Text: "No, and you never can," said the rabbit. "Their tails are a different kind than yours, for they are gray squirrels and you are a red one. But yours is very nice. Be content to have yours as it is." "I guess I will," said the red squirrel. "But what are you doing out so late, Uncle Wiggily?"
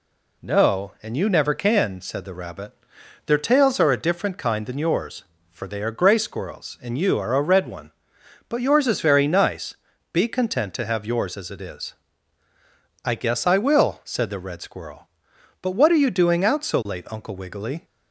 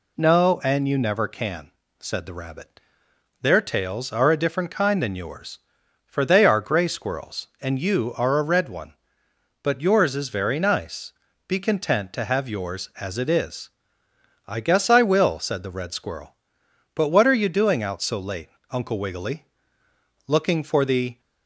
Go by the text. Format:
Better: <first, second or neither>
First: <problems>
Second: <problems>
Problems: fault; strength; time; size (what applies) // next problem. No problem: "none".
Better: first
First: none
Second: goes on to say "Looking for the"; noticeable; from 20.2 s on; 0.94 s long